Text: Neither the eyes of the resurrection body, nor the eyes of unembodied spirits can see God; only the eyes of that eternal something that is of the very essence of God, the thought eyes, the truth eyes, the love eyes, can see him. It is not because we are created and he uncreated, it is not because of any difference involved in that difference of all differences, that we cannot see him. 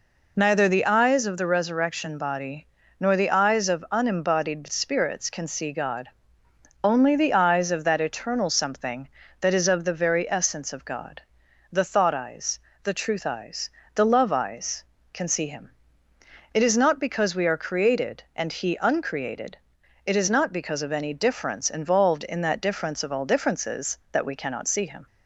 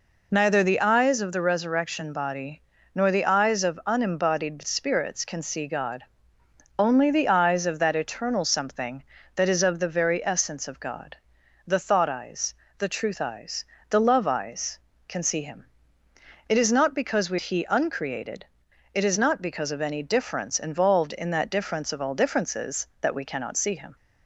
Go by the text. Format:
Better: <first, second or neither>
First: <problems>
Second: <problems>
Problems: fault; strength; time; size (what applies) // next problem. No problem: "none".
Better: first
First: none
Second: skips "are created and"; at 17.3 s